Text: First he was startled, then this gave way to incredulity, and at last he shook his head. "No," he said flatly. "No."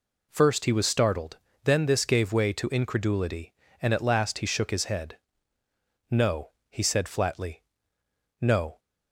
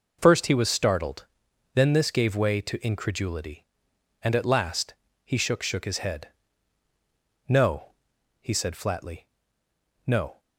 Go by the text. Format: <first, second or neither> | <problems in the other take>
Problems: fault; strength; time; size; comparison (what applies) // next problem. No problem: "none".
first | pauses between "last" and "he"; slight; at 4.9 s; 0.30 s long // says "shook" twice; at 5.6 s